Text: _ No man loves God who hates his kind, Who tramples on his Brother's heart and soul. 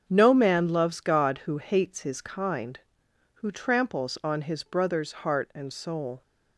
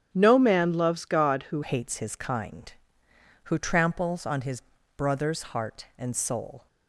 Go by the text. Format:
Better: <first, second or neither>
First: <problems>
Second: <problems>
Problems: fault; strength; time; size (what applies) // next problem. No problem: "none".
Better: first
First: starts louder than the rest; until 1.0 s; 7 dB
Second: starts louder than the rest; strong; until 1.1 s; 9.5 dB // changes voice at "hates"; from 1.6 s on; 5.0 s long // pauses between "his" and "Brother's"; slight; at 4.6 s; 0.32 s long